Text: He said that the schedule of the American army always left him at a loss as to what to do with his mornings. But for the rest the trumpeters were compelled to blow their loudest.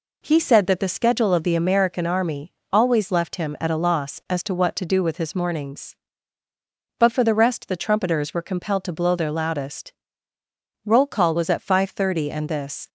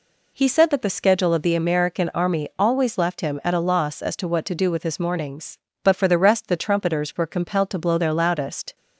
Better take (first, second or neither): second